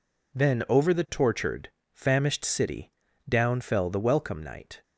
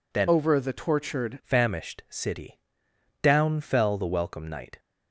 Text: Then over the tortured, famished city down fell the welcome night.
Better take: first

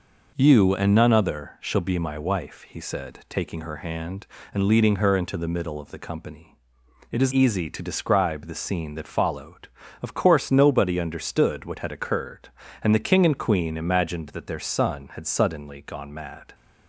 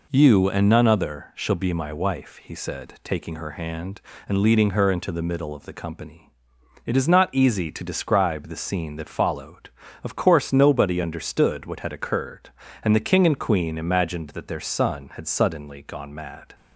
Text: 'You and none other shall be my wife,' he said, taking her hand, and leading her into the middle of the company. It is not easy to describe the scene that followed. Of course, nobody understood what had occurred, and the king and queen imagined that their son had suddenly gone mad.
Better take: second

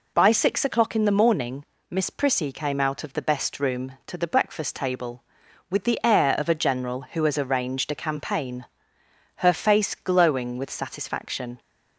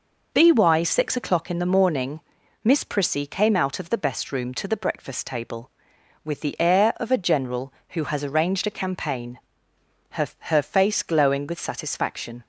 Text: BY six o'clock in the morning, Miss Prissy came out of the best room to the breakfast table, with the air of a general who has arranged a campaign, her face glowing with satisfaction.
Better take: first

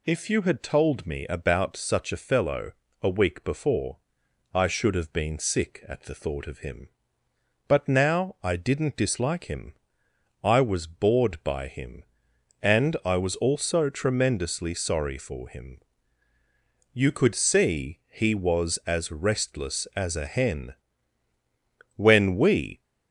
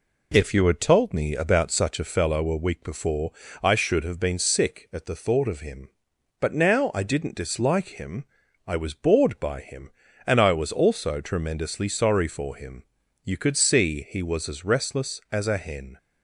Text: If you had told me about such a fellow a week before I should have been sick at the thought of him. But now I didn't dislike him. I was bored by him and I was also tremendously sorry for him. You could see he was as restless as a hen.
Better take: second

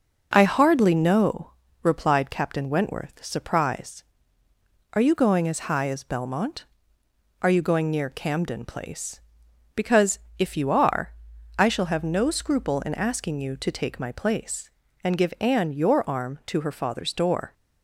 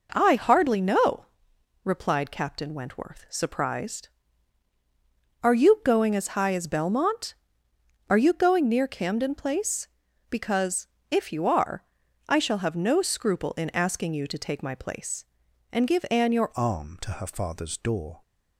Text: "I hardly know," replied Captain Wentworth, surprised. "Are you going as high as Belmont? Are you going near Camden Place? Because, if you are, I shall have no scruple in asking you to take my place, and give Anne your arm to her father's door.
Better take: first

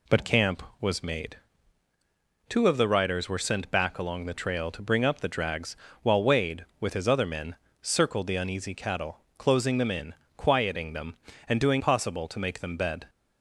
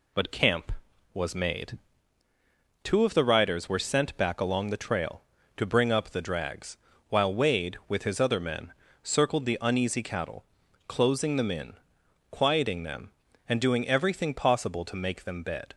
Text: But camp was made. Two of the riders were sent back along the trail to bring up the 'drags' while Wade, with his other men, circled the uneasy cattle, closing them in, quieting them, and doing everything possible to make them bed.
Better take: second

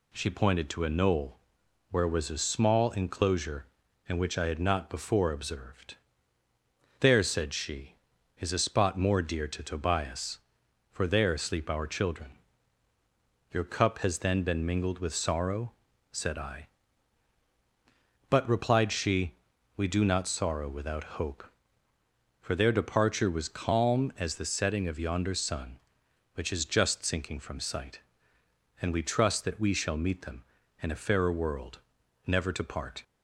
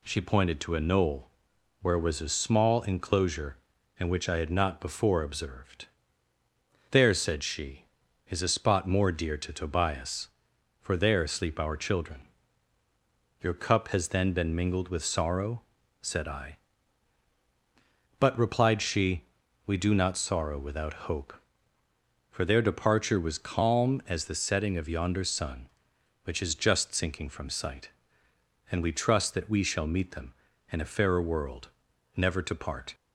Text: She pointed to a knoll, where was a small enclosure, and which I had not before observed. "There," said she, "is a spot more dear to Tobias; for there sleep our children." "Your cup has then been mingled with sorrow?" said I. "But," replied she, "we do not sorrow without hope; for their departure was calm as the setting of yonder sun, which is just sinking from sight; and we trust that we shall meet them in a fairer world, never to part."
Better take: neither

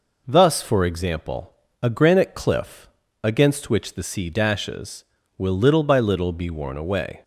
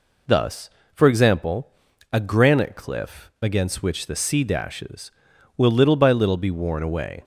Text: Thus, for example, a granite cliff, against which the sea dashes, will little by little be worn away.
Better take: neither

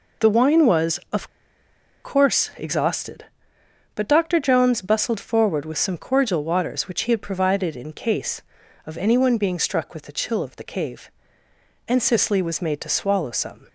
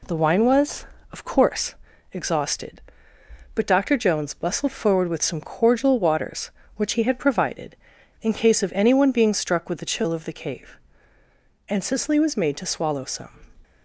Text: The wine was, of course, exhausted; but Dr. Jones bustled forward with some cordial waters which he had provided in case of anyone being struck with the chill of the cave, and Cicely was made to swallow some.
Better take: second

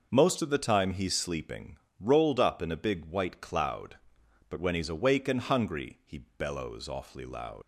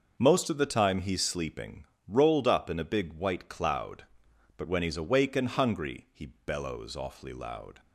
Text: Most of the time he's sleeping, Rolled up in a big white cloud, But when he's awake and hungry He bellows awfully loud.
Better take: second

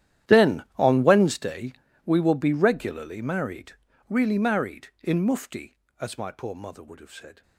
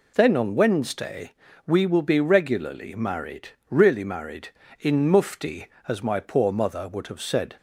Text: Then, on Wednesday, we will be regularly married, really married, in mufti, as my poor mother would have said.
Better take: second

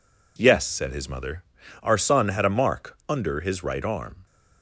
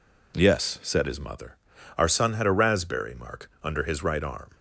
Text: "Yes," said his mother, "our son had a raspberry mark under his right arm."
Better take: second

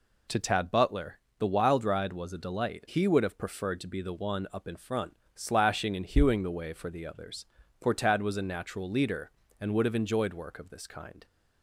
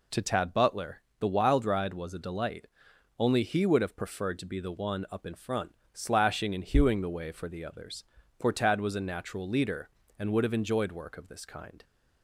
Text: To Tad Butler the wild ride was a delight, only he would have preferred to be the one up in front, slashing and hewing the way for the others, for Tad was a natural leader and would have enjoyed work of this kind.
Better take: second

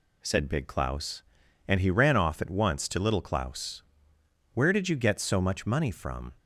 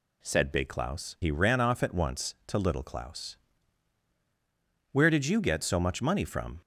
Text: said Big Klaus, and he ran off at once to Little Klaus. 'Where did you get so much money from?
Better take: first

